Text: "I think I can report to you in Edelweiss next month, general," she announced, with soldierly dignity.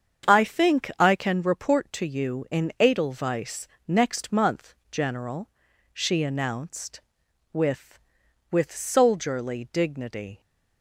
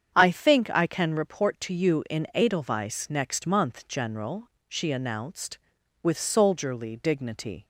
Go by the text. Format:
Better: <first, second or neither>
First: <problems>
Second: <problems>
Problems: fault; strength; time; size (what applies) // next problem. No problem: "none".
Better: second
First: starts louder than the rest; strong; until 1.3 s; 7.5 dB // pauses between "Edelweiss" and "next"; slight; at 3.6 s; 0.18 s long // says "with" twice; at 8.5 s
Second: starts louder than the rest; strong; until 1.1 s; 8 dB